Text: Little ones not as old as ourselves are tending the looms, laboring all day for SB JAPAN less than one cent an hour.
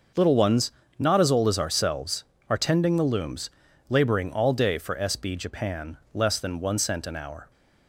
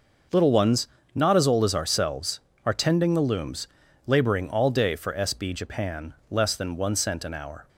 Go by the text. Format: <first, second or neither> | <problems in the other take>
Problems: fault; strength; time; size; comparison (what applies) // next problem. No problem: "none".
neither | starts louder than the rest; noticeable; the same in both // pauses between "ones" and "not"; slight; the same in both // pauses between "JAPAN" and "less"; slight; the same in both